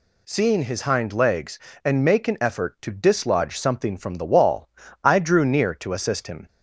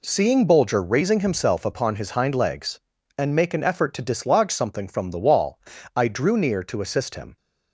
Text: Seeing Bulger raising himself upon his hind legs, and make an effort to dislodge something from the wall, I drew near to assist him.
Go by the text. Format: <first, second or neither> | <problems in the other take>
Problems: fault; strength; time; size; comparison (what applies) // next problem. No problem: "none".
second | skips "Bulger raising himself upon"; at 0.6 s